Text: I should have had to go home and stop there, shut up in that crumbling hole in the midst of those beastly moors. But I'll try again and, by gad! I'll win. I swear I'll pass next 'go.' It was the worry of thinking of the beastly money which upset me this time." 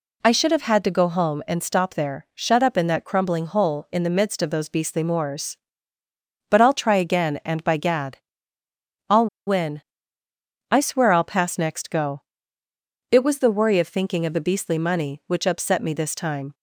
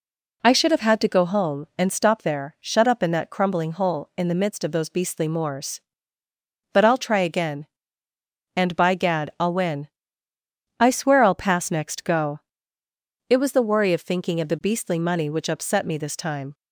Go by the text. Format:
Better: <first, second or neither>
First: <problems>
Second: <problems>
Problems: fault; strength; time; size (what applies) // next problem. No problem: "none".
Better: second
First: pauses between "I'll" and "win"; slight; at 9.2 s; 0.20 s long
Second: none